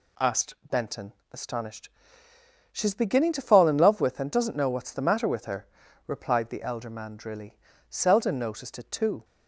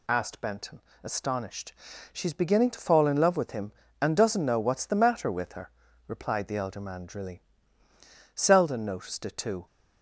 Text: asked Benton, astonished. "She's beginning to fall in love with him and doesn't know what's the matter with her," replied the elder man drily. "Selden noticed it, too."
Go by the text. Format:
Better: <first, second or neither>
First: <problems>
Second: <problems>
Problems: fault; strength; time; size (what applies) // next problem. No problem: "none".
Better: second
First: pauses between "asked" and "Benton"; slight; at 0.5 s; 0.16 s long // skips "him"; at 4.2 s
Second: none